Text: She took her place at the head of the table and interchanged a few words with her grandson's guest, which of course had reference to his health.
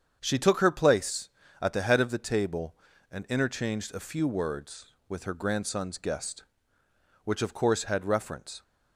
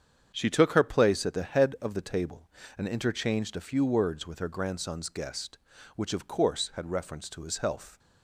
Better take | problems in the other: second | starts louder than the rest; strong; until 1.2 s; 7.5 dB; strong in the second // stops before "to his health"; at 8.6 s

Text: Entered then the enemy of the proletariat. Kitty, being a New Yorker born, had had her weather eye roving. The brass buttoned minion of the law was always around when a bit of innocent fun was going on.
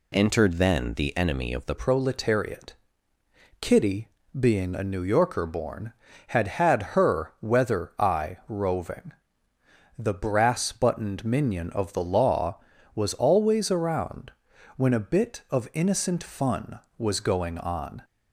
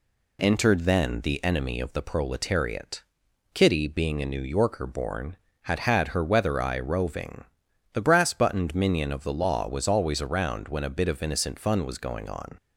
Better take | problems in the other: second | changes voice at "proletariat"; from 1.7 s on; 16.3 s long // pauses between "around" and "when"; noticeable; at 14.3 s; 0.46 s long

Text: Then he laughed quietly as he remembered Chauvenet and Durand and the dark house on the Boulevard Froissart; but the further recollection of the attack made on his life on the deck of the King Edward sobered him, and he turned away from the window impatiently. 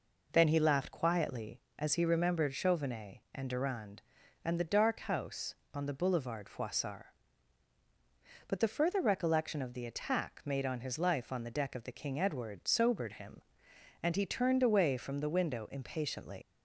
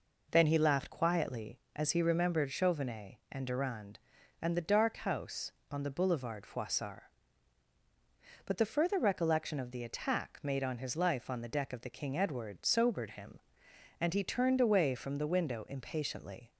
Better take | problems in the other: second | leaves "impatiently" unfinished; at 16.4 s; 115 ms

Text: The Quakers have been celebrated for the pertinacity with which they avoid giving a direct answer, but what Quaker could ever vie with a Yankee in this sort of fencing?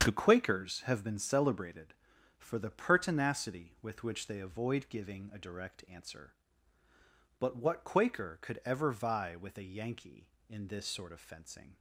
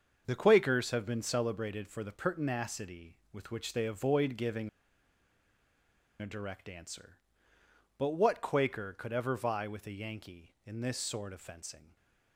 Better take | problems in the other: first | starts louder than the rest; until 1.2 s; 6.5 dB; strong in the first // pauses between "giving" and "a"; strong; at 4.6 s; 1.5 s long // stays silent after the last word; slight; from 11.8 s on; 0.5 s long

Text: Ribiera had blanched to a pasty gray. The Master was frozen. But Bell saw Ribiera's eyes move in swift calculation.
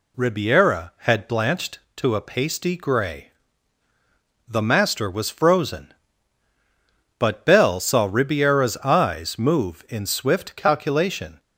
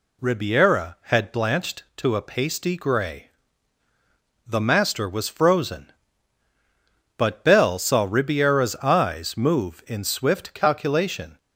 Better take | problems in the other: neither | none

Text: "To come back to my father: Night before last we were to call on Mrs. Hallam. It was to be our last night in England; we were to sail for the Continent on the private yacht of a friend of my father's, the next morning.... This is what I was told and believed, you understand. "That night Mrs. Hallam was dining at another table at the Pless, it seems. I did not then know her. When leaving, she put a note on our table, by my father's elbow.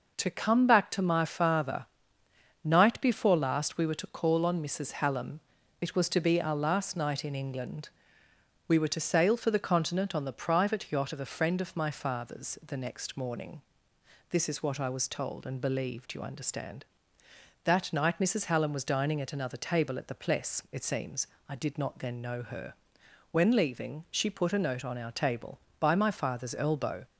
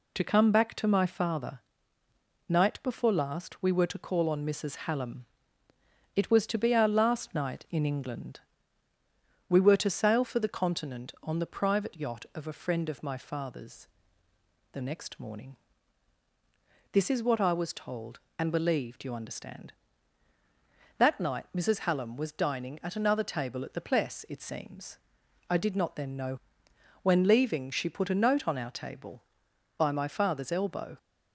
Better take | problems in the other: first | skips "her"; at 26.6 s

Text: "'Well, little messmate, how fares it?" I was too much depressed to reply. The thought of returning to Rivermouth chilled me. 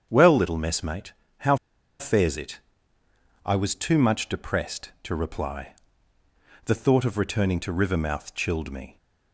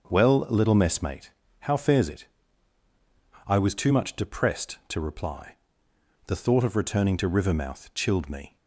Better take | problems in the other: second | starts louder than the rest; strong; until 1.1 s; 7.5 dB; also in the second // pauses between "how" and "fares"; at 1.5 s; 0.43 s long

